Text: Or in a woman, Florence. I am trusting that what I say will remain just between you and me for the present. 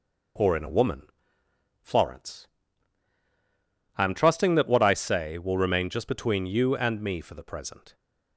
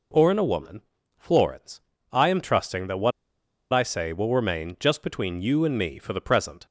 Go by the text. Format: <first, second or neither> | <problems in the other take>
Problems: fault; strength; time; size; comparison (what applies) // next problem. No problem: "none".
first | pauses between "what" and "I"; noticeable; at 3.1 s; 0.62 s long